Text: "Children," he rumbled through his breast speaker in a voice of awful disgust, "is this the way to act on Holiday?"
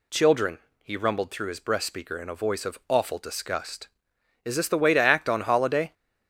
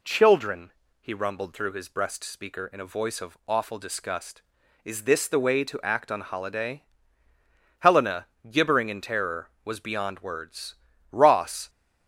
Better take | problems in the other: first | goes on to say "Helena gibbering in terror was beyond words Ross"; strong; from 7.7 s on; 3.9 s long

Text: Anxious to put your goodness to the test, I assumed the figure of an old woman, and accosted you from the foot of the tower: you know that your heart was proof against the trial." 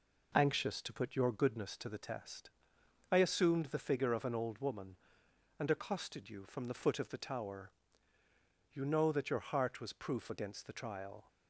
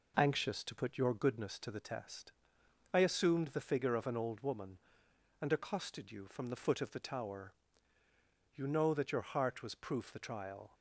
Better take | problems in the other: first | skips "against"; at 10.1 s

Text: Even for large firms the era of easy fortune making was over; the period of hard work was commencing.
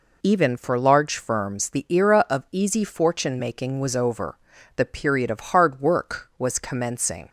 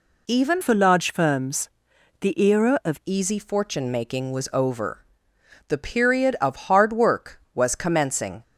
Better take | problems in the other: first | changes voice from "for" to "of"; from 0.6 to 2.9 s; 2.3 s long // pauses between "firms" and "the"; noticeable; at 1.6 s; 0.52 s long

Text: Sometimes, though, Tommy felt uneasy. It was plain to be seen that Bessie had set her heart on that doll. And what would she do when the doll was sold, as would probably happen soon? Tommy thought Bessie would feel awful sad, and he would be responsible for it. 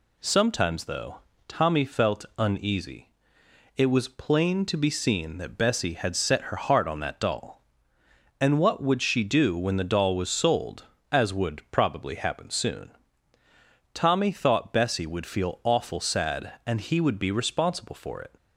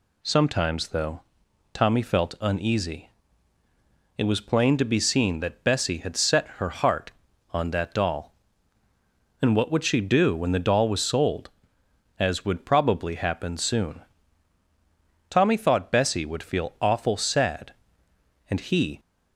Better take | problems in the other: first | stops before "would be responsible for it"; at 18.9 s

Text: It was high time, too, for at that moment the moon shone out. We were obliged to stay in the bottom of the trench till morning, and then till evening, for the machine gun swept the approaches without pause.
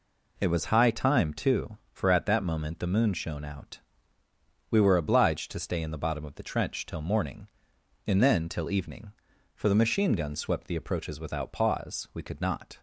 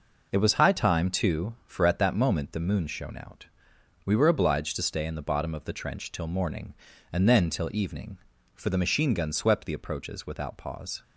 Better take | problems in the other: second | goes on to say "We could not"; noticeable; from 12.1 s on; 0.66 s long

